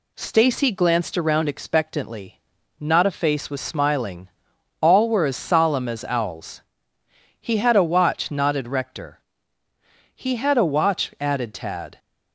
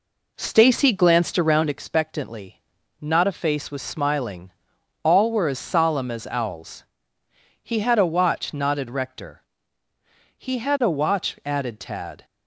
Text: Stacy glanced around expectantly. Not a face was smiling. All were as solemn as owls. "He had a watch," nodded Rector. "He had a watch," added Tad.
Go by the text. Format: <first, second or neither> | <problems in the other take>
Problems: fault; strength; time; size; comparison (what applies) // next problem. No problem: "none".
first | starts louder than the rest; until 1.8 s; 3.5 dB